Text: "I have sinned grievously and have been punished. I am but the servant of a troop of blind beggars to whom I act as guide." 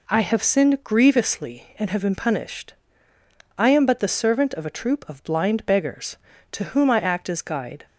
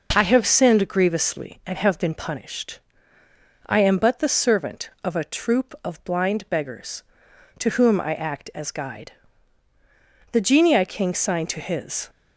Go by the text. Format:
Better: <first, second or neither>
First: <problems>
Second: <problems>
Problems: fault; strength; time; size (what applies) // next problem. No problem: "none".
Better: first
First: none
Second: goes on to say "The genii king signed to his"; strong; from 10.3 s on; 1.7 s long